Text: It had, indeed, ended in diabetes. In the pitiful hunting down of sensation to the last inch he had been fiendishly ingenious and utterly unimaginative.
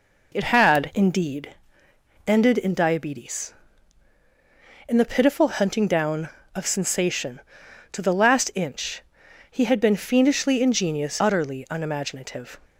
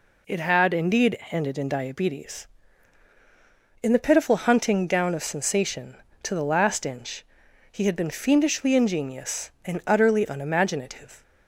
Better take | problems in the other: second | pauses between "inch" and "he"; noticeable; at 9.0 s; 0.48 s long; noticeable in the second // skips "and"; at 11.1 s

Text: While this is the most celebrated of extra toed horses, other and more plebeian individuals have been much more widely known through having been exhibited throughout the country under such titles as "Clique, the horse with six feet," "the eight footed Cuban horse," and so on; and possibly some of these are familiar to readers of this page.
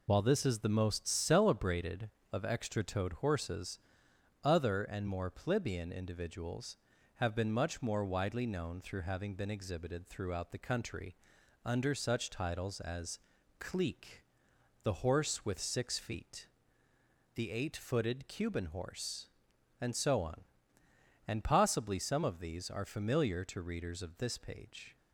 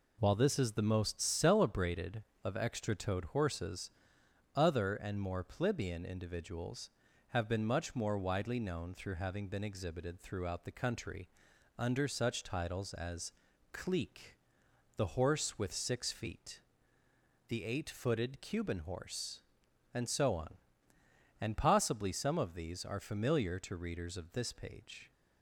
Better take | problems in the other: second | loses the start of "While"; at 0.0 s; 35 ms // pauses between "country" and "under"; noticeable; at 11.1 s; 0.50 s long; noticeable in the second // pauses between "as" and "Clique"; at 13.1 s; 0.40 s long; also in the second

